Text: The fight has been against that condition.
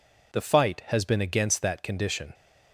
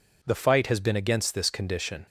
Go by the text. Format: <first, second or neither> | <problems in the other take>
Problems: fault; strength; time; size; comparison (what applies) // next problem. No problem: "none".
first | says "this" for "that"; at 1.3 s